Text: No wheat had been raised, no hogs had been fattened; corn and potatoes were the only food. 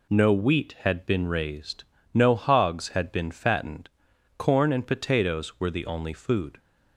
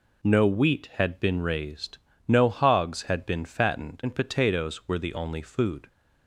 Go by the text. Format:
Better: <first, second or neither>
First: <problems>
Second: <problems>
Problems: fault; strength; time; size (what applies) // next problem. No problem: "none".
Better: first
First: none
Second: skips "corn"; at 4.0 s